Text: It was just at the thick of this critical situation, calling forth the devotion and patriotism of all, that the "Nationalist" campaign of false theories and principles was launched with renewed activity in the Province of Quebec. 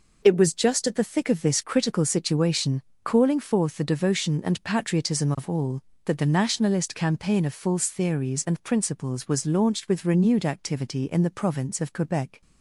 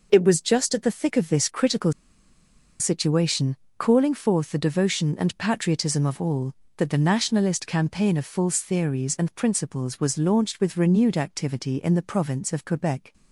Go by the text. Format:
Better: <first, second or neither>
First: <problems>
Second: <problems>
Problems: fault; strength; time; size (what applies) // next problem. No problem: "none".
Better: first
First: none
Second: pauses between "critical" and "situation"; noticeable; at 1.9 s; 0.87 s long